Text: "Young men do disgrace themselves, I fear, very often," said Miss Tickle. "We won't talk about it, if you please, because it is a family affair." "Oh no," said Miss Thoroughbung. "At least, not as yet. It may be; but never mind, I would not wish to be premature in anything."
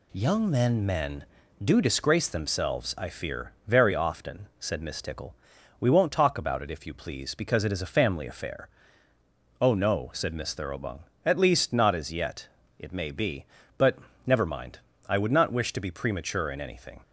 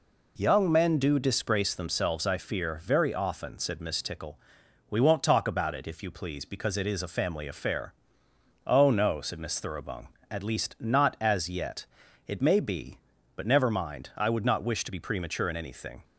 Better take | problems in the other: second | says "men" twice; at 0.8 s // pauses between "but" and "never"; slight; at 13.9 s; 0.26 s long

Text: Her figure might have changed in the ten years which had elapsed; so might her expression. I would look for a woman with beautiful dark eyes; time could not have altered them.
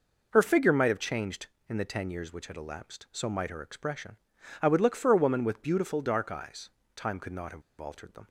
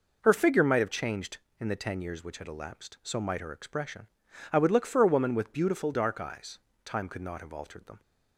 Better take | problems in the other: second | pauses between "have" and "altered"; slight; at 7.6 s; 0.18 s long

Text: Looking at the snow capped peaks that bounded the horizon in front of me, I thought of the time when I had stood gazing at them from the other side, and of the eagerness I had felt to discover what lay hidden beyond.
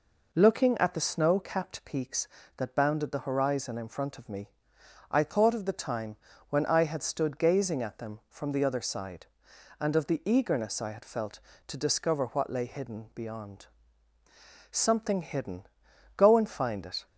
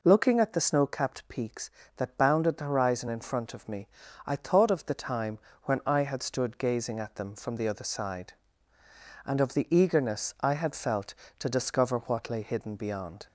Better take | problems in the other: second | pauses between "time" and "when"; slight; at 6.1 s; 0.34 s long; slight in the second // goes on to say "Something hidden Go and find it"; strong; from 14.6 s on; 2.3 s long

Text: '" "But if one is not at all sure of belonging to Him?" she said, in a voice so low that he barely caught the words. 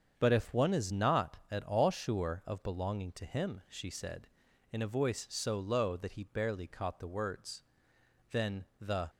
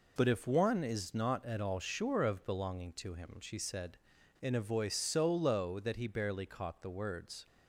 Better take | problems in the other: second | starts louder than the rest; until 1.1 s; 7 dB // goes on to say "Then the"; noticeable; from 8.2 s on; 0.80 s long

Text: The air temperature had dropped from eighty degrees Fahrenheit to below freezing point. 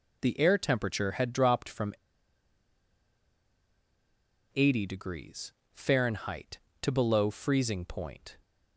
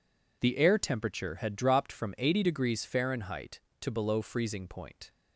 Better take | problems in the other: second | pauses between "from" and "eighty"; strong; at 1.9 s; 2.6 s long // pauses between "degrees" and "Fahrenheit"; slight; at 5.5 s; 0.22 s long

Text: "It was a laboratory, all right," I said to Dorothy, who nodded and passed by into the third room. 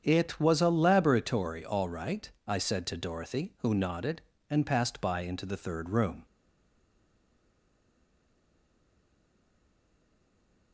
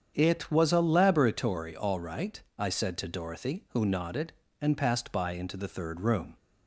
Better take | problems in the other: second | starts louder than the rest; strong; until 1.0 s; 7.5 dB; strong in the second // stays silent after the last word; strong; from 6.2 s on; 4.5 s long

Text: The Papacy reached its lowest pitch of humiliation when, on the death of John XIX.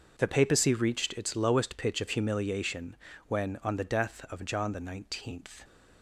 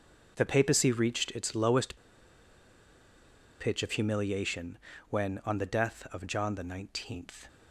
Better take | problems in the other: first | pauses between "lowest" and "pitch"; strong; at 1.9 s; 1.6 s long // pauses between "humiliation" and "when"; slight; at 4.7 s; 0.32 s long; slight in the first

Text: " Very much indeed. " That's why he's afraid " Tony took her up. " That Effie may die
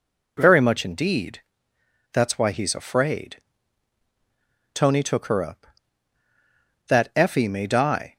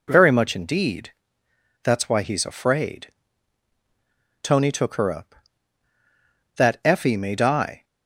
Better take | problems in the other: neither | none

